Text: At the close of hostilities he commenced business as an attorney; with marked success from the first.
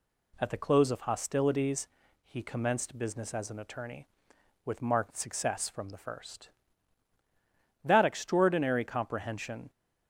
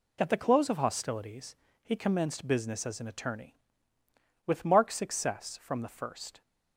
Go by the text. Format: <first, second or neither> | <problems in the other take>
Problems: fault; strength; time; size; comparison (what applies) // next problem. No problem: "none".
second | pauses between "hostilities" and "he"; at 1.8 s; 0.42 s long; slight in the second // goes on to say "That extraordinary comprehension"; strong; from 7.8 s on; 1.8 s long